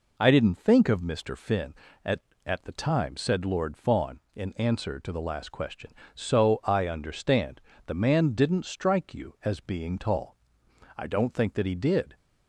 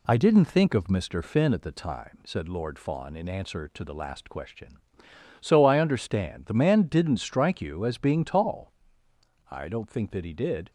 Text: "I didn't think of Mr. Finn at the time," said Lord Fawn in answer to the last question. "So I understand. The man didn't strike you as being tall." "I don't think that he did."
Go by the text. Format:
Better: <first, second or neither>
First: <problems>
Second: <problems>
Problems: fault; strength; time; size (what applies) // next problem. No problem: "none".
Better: second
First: says "at" twice; at 2.4 s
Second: none